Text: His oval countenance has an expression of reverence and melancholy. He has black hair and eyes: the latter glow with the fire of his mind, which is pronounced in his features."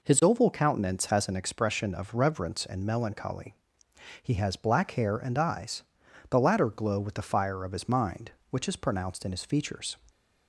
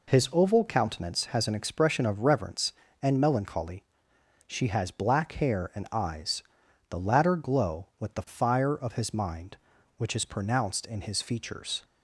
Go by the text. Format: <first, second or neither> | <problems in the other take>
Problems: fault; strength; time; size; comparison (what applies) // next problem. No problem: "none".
first | says "She" for "He"; at 4.4 s